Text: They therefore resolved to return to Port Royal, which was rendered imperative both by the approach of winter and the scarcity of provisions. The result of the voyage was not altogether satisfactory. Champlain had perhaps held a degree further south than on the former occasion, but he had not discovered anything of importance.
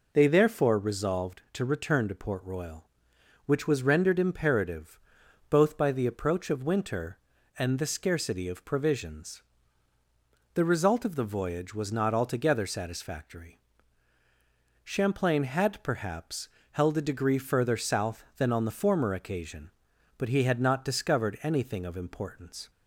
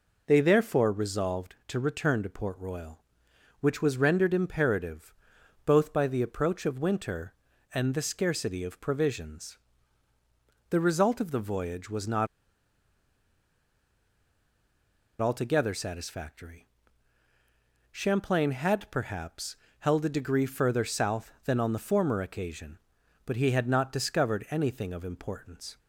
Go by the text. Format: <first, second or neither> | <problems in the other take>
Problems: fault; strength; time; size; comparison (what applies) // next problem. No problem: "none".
first | pauses between "imperative" and "both"; noticeable; at 5.1 s; 0.50 s long; noticeable in the first // pauses between "not" and "altogether"; strong; at 12.2 s; 2.9 s long // pauses between "perhaps" and "held"; slight; at 19.5 s; 0.24 s long; slight in the first